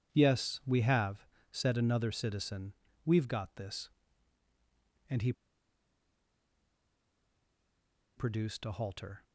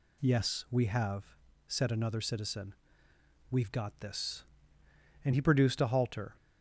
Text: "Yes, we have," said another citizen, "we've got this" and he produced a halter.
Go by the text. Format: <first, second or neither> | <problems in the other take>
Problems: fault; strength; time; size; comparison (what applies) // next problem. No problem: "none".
second | pauses between "he" and "produced"; strong; at 5.3 s; 2.8 s long